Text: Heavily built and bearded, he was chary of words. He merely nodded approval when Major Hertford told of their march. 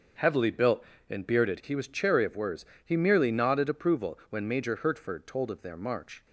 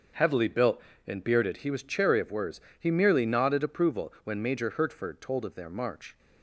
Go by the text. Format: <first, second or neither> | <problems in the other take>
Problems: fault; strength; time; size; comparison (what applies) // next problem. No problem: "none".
neither | starts louder than the rest; the same in both